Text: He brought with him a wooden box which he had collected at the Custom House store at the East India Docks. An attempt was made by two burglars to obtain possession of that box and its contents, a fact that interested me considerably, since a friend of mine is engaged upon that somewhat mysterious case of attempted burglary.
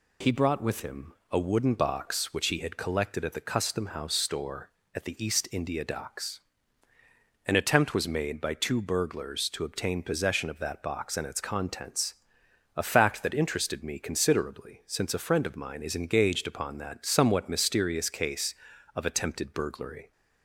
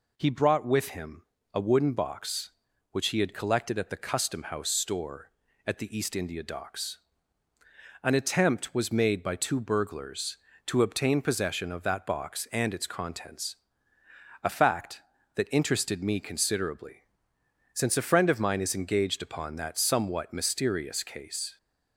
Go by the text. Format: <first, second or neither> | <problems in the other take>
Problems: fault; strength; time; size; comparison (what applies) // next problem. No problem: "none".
first | pauses between "him" and "a"; slight; at 1.2 s; 0.30 s long; slight in the first // stops before "of attempted burglary"; at 21.5 s